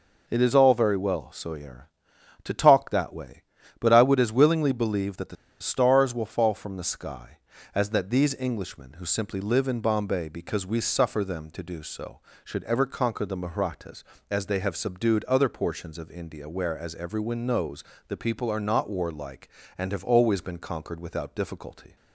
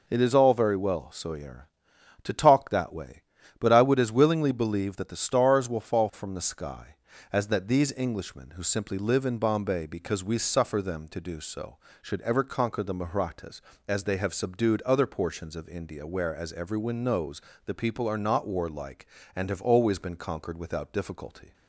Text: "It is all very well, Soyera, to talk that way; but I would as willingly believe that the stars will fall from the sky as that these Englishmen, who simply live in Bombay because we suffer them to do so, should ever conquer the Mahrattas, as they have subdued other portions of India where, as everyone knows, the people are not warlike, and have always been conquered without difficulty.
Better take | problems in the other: second | pauses between "the" and "stars"; slight; at 5.3 s; 0.25 s long

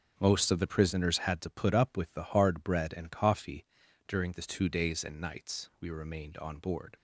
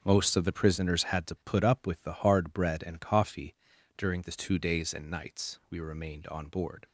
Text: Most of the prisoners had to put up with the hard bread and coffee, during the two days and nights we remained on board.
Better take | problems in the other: neither | none

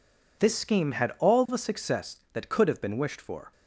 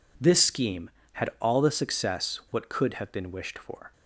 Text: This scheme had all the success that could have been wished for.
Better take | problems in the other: first | says "what" for "that"; at 2.5 s

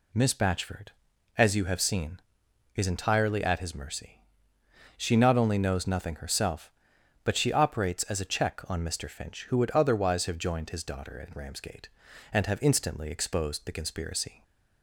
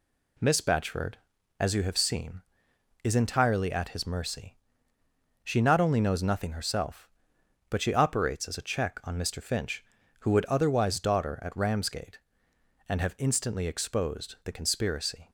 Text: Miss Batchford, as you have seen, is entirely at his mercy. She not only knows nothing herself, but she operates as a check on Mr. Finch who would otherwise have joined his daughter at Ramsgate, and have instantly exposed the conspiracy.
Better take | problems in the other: first | skips "have joined his"; at 10.9 s

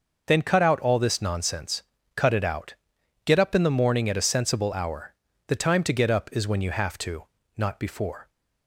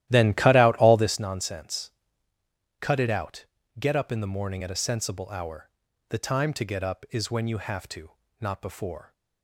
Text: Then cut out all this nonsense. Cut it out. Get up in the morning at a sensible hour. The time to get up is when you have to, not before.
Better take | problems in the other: first | starts louder than the rest; strong; until 1.3 s; 13.5 dB

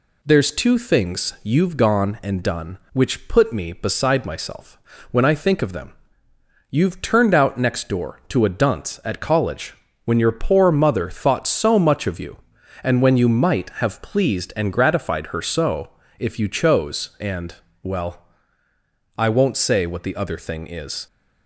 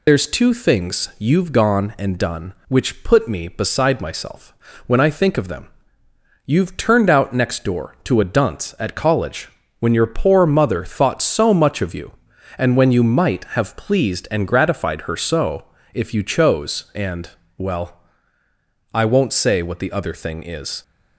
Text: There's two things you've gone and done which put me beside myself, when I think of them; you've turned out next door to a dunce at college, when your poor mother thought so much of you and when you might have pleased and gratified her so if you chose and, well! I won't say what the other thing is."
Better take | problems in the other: first | loses the start of "There's"; at 0.0 s; 85 ms // pauses between "so" and "if"; slight; at 15.6 s; 0.30 s long; slight in the first

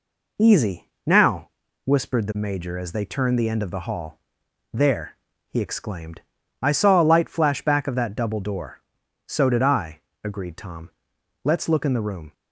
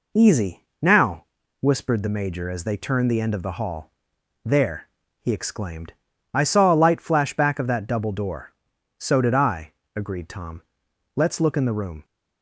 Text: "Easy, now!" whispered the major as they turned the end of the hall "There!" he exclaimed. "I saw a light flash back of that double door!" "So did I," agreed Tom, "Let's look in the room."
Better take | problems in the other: neither | pauses between "hall" and "There"; noticeable; the same in both

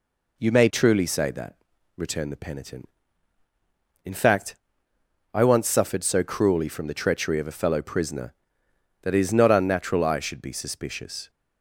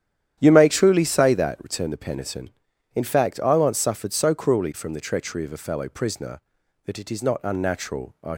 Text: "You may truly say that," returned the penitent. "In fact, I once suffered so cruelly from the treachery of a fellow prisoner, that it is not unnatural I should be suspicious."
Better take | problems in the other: first | starts louder than the rest; strong; until 1.4 s; 10 dB // stops before "should be suspicious"; at 8.3 s

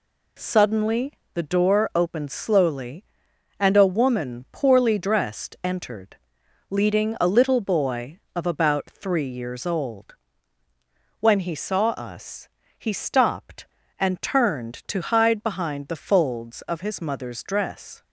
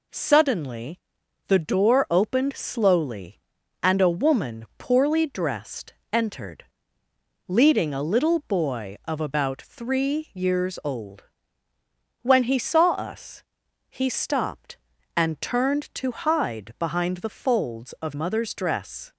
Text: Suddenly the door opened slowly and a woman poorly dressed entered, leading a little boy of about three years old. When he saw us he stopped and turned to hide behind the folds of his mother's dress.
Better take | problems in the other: first | pauses between "Suddenly" and "the"; noticeable; at 0.9 s; 0.48 s long; slight in the first // pauses between "dressed" and "entered"; slight; at 5.9 s; 0.18 s long // pauses between "us" and "he"; noticeable; at 13.4 s; 0.48 s long; slight in the first // skips "his"; at 18.1 s

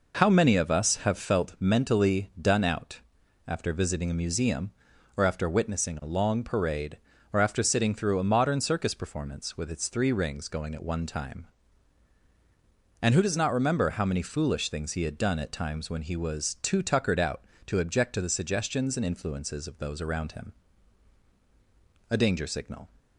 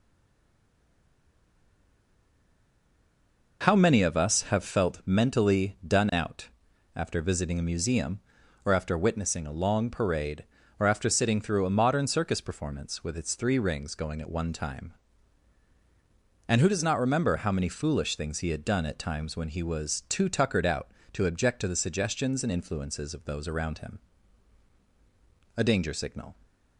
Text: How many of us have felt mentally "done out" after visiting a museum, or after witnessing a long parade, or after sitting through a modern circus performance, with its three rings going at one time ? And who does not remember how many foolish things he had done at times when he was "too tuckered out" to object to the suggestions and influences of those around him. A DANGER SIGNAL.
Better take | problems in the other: first | stays silent before the first word; strong; until 3.6 s; 3.6 s long // pauses between "out" and "after"; noticeable; at 6.4 s; 0.46 s long; noticeable in the first

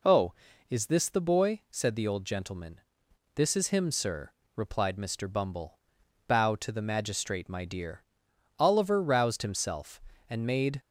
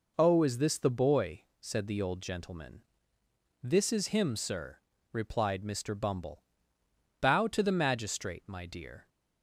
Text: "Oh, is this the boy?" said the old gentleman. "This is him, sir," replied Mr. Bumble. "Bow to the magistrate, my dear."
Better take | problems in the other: second | goes on to say "Oliver roused himself and made"; strong; from 8.5 s on; 2.2 s long

